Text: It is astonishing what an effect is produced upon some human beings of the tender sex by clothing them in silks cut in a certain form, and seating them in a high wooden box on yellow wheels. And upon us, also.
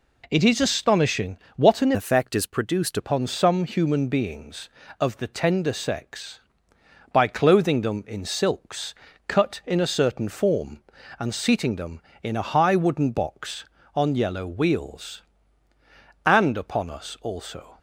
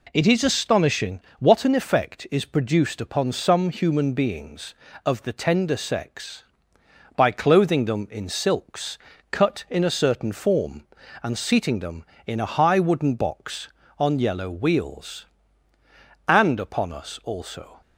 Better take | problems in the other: second | pauses between "astonishing" and "what"; slight; at 1.3 s; 0.20 s long; slight in the second // changes voice from "effect" to "produced"; from 1.9 to 2.9 s; 1.0 s long // pauses between "silks" and "cut"; slight; at 8.9 s; 0.34 s long; slight in the second

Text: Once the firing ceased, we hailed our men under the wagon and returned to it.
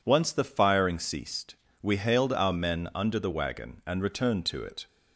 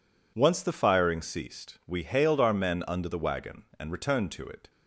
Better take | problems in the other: neither | none

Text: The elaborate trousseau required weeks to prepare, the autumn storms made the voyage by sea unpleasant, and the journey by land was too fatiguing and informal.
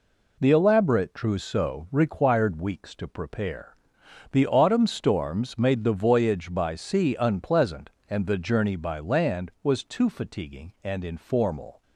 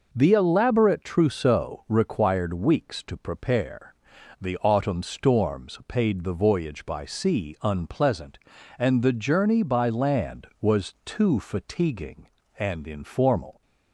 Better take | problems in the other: first | says "paid" for "made"; at 5.8 s

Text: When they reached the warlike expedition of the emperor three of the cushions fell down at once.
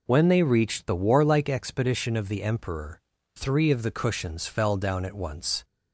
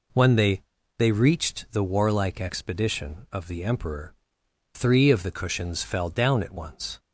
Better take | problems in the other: first | says "they" twice; at 0.9 s // pauses between "emperor" and "three"; noticeable; at 4.1 s; 0.60 s long; slight in the first

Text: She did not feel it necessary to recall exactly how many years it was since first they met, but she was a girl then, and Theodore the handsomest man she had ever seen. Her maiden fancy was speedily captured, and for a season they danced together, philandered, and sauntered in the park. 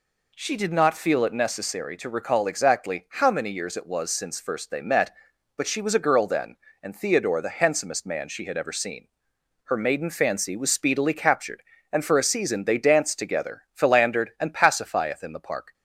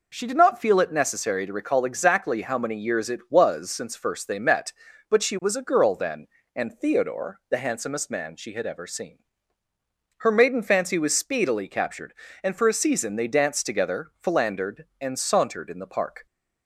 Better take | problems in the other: second | says "pacifieth" for "sauntered"; at 14.5 s

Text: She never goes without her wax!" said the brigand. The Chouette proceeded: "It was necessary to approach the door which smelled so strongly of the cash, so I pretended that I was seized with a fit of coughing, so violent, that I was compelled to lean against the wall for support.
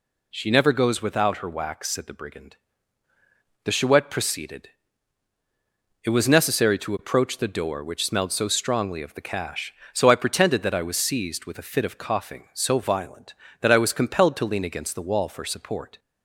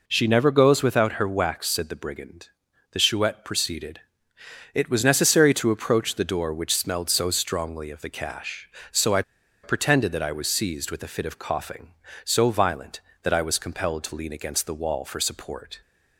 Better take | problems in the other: first | pauses between "I" and "pretended"; at 9.2 s; 0.39 s long

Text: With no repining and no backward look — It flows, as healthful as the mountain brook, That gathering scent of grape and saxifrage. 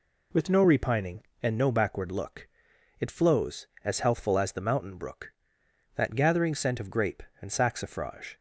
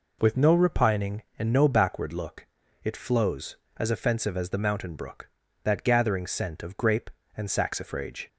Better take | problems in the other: first | says "offensive" for "healthful"; at 3.8 s

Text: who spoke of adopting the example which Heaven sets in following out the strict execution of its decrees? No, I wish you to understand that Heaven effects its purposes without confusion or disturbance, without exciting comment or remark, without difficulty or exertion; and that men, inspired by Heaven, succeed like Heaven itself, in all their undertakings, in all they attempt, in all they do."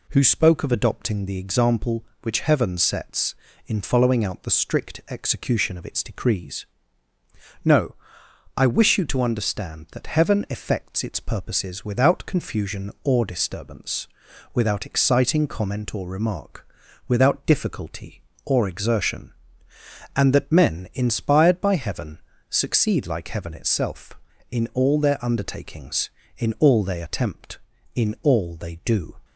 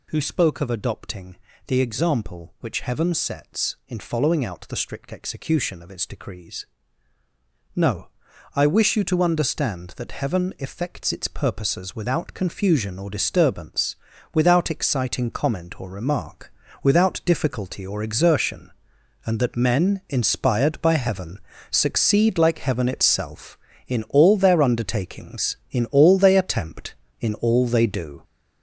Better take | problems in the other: first | gets louder; throughout; 6.5 dB // pauses between "adopting" and "the"; slight; at 1.3 s; 0.30 s long

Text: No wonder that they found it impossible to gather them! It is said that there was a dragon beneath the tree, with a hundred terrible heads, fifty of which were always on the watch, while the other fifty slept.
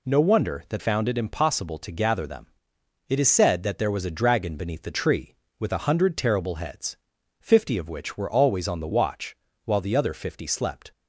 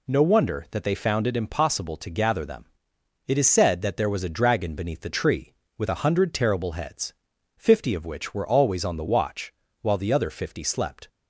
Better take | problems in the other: second | skips "they"; at 0.8 s

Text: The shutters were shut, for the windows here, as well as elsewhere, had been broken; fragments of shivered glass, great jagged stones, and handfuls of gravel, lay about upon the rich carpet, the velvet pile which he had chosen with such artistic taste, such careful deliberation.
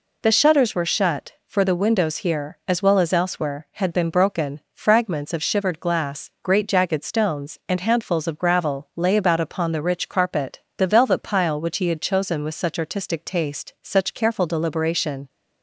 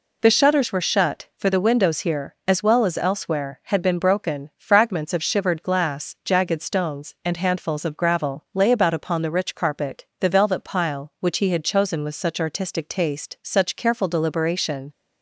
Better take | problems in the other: first | skips "great"; at 6.2 s

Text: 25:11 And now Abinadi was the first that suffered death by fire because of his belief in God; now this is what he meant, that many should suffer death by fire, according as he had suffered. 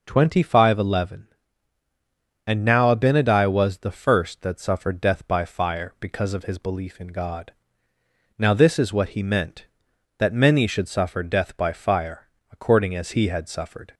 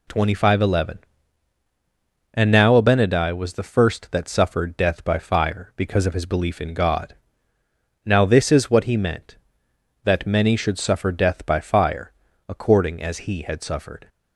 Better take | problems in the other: neither | none

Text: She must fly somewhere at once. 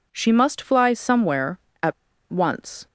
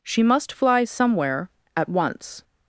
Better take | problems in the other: second | pauses between "at" and "once"; at 1.9 s; 0.37 s long

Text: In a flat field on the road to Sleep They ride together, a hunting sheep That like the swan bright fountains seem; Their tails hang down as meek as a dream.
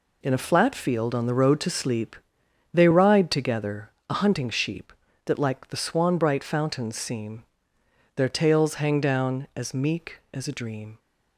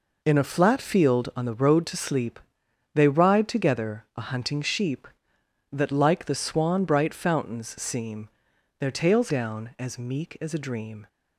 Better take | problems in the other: first | pauses between "Sleep" and "They"; noticeable; at 2.3 s; 0.56 s long; noticeable in the first // skips "hang"; at 9.2 s

